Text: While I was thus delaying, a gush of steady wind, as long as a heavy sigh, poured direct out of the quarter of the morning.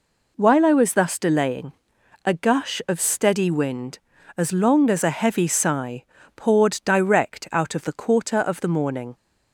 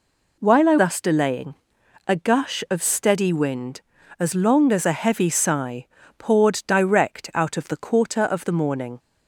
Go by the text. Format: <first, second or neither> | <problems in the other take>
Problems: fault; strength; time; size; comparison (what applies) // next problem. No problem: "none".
first | skips "was"; at 0.7 s